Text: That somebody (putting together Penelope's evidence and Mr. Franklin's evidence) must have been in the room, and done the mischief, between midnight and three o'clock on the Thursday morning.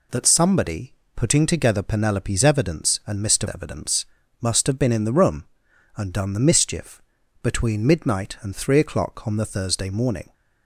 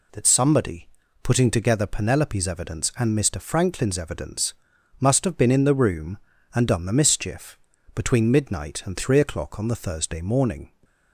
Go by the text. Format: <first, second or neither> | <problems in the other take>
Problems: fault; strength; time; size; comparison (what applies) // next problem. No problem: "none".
second | skips "Franklin's"; at 3.4 s